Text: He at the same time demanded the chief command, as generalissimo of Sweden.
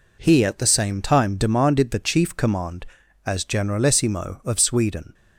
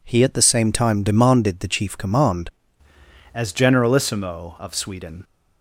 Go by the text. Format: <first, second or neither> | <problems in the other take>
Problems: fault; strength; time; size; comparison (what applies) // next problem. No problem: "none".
first | changes voice at "as"; from 3.3 s on; 1.9 s long